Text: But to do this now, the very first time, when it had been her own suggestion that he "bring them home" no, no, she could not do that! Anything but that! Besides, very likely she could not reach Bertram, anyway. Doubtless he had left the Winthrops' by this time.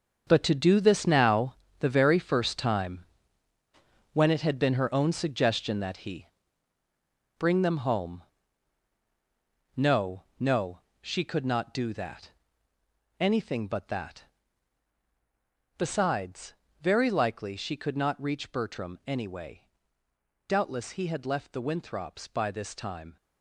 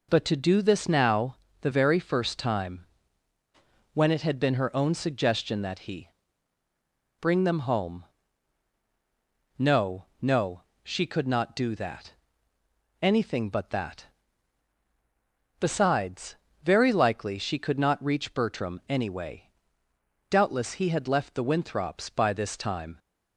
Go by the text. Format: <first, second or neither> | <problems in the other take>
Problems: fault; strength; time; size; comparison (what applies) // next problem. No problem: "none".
second | gets quieter; strong; throughout; 10.5 dB // pauses between "he" and "bring"; at 6.2 s; 1.1 s long; also in the second // pauses between "home" and "no"; strong; at 8.2 s; 1.5 s long; strong in the second